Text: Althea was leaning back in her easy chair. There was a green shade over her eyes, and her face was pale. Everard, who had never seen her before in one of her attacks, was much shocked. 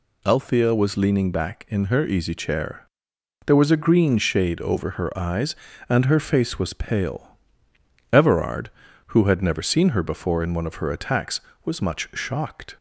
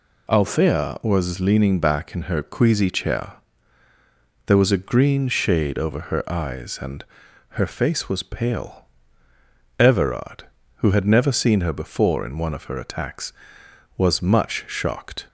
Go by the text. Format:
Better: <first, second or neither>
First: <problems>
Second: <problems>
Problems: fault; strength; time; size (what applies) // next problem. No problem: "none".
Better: first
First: none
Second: says "queasy" for "easy"; at 2.4 s // pauses between "and" and "her"; noticeable; at 7.0 s; 0.46 s long